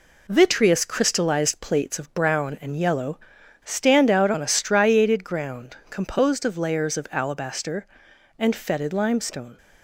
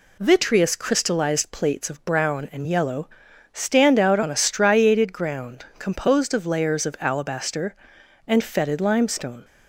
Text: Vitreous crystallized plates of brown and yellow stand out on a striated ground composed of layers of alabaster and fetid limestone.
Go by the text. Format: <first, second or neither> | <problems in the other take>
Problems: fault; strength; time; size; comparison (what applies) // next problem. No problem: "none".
second | gets quieter; noticeable; throughout; 4.5 dB // pauses between "yellow" and "stand"; noticeable; at 3.1 s; 0.46 s long; also in the second